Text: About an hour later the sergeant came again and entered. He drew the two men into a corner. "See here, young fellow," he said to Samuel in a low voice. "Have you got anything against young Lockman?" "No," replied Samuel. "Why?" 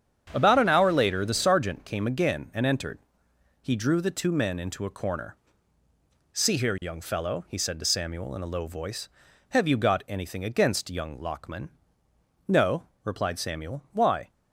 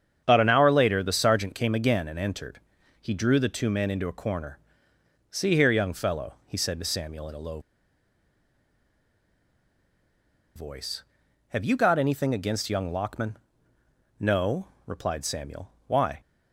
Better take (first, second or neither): first